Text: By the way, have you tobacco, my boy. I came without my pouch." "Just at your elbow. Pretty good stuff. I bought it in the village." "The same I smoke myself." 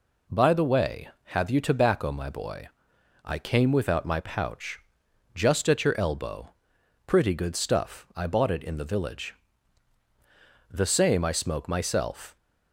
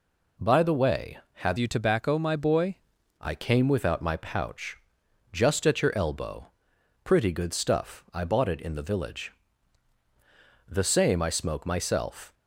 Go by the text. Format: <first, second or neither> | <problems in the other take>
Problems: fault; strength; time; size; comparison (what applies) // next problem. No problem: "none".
first | changes voice from "you" to "boy"; from 1.5 to 2.7 s; 1.2 s long